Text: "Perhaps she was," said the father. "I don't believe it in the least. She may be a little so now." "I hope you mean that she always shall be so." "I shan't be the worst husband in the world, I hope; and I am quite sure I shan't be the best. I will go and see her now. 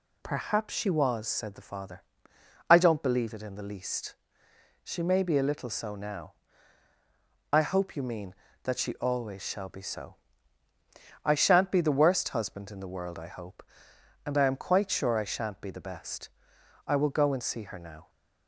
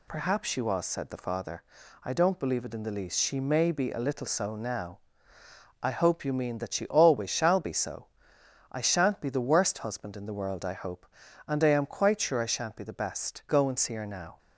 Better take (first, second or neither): first